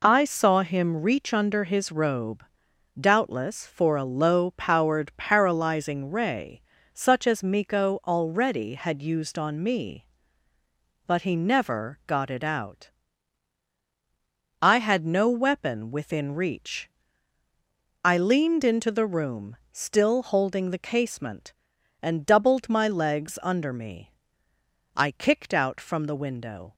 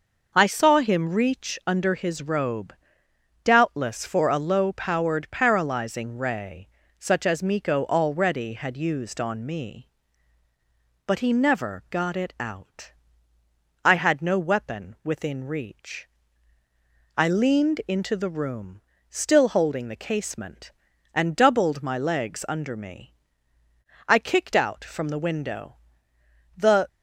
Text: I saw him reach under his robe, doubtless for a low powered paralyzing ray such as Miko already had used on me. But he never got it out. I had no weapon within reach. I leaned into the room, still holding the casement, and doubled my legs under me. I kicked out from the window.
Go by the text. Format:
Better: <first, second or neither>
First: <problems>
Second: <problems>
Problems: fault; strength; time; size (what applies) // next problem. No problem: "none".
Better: first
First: pauses between "ray" and "such"; slight; at 6.6 s; 0.34 s long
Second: pauses between "ray" and "such"; slight; at 6.6 s; 0.30 s long // goes on to say "The"; slight; from 26.5 s on; 0.32 s long